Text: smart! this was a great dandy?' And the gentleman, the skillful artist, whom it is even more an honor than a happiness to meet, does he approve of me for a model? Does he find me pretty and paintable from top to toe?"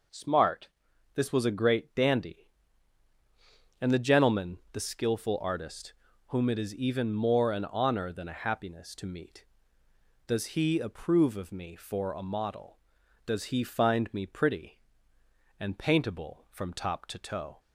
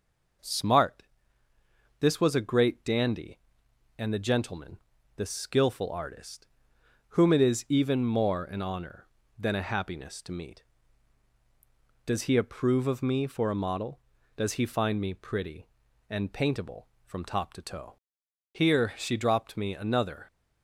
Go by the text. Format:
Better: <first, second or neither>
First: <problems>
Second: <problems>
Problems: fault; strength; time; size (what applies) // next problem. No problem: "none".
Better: first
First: none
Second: goes on to say "Here she dropped me another"; strong; from 18.5 s on; 1.7 s long